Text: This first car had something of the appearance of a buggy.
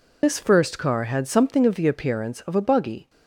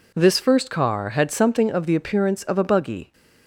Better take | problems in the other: second | loses the start of "This"; at 0.2 s; 75 ms

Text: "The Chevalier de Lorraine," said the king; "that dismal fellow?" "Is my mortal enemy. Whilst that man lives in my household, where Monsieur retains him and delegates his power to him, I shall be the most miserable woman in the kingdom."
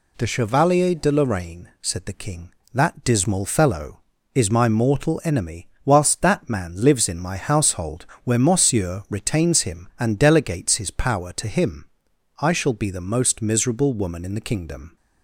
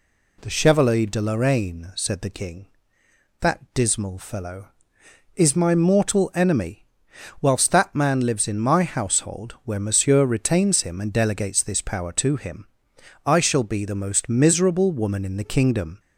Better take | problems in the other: first | says "this" for "his"; at 11.6 s

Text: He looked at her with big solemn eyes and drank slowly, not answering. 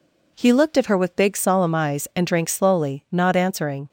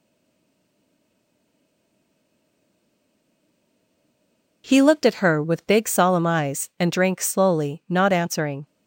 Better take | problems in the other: first | stays silent before the first word; strong; until 4.6 s; 4.6 s long

